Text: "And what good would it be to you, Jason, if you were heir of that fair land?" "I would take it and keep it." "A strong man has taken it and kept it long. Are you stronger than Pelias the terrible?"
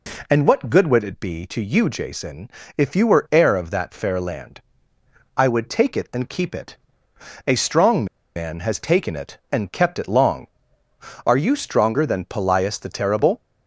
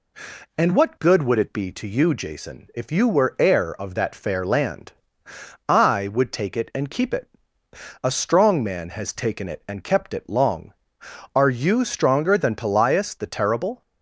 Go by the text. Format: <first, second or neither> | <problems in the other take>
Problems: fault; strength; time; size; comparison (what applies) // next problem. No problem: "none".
second | pauses between "strong" and "man"; slight; at 8.0 s; 0.30 s long